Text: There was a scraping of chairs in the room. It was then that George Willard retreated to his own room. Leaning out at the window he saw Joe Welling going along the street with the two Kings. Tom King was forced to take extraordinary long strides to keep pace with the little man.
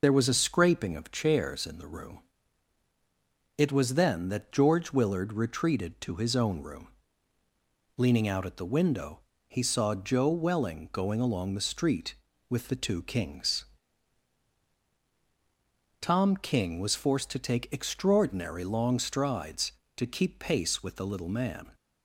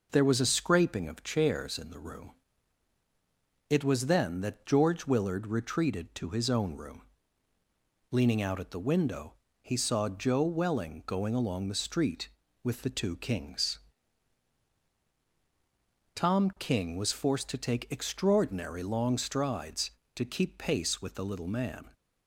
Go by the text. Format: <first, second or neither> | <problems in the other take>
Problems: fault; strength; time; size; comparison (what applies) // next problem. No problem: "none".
second | loses the start of "There"; at 0.0 s; 35 ms // pauses between "window" and "he"; slight; at 9.2 s; 0.26 s long; slight in the second